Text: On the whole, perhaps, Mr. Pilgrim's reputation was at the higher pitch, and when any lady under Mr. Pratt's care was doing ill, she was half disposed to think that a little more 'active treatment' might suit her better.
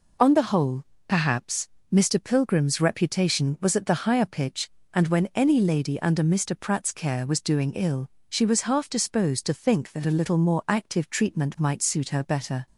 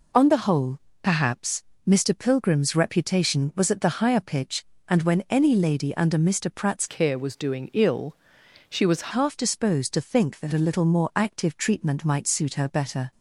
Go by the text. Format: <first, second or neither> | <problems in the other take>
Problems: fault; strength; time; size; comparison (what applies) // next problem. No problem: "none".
first | changes voice from "care" to "was"; from 6.8 to 9.1 s; 2.3 s long